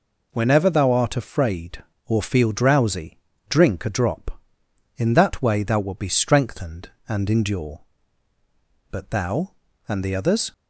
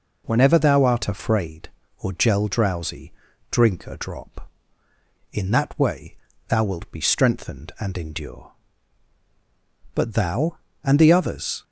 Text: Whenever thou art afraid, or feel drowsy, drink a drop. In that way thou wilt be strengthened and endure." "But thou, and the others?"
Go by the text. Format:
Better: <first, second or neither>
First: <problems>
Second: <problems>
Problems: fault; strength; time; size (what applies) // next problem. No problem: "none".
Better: first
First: none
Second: says "gel" for "feel"; at 2.1 s // pauses between "way" and "thou"; slight; at 6.1 s; 0.32 s long